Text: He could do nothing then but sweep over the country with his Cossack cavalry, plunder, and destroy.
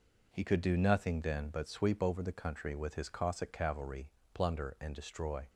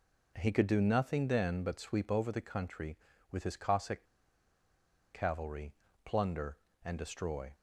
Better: first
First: none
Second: pauses between "Cossack" and "cavalry"; at 4.0 s; 1.0 s long

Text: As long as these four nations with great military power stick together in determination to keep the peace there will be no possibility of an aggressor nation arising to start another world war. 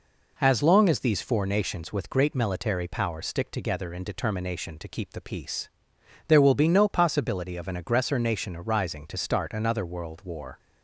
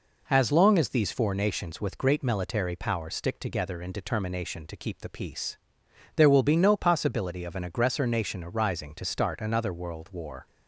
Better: neither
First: pauses between "peace" and "there"; noticeable; at 5.6 s; 0.58 s long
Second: pauses between "peace" and "there"; noticeable; at 5.5 s; 0.58 s long

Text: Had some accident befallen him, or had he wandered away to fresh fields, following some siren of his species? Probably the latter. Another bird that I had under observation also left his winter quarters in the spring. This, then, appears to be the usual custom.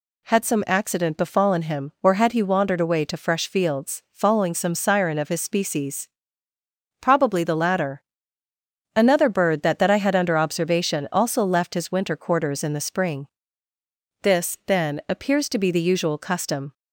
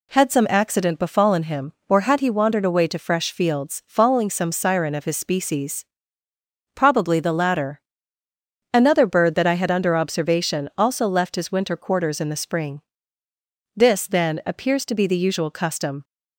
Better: second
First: says "that" twice; at 9.7 s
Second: none

